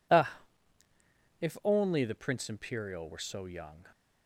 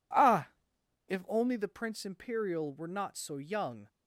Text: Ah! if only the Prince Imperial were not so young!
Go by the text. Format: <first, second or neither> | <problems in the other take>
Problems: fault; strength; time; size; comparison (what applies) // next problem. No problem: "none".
second | skips "not"; at 3.1 s